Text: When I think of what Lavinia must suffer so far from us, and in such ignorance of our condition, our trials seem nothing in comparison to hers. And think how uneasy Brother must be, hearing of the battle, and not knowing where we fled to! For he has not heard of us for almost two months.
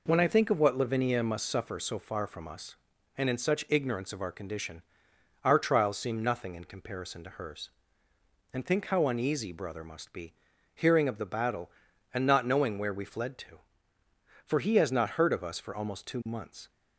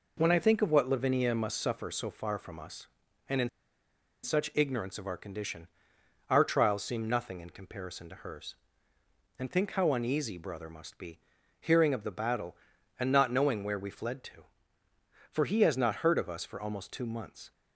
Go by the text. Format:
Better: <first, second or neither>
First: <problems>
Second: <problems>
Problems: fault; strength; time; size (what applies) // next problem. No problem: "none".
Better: first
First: none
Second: pauses between "in" and "such"; noticeable; at 3.4 s; 0.75 s long